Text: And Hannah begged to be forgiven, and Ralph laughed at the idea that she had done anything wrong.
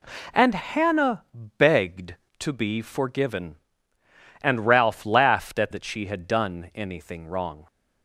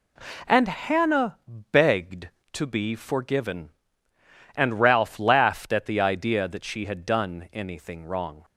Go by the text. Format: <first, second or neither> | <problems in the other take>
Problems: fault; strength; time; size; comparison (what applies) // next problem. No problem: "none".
second | pauses between "Hannah" and "begged"; slight; at 1.2 s; 0.34 s long; slight in the second // skips "the idea"; at 5.7 s